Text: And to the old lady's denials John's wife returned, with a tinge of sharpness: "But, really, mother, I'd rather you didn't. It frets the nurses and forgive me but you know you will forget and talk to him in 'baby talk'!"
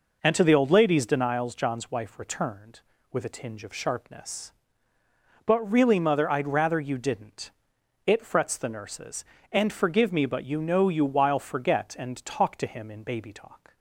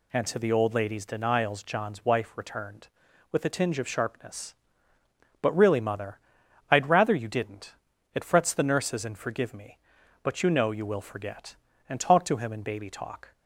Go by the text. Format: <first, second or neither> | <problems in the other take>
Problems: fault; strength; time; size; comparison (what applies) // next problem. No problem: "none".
second | says "while" for "will"; at 11.0 s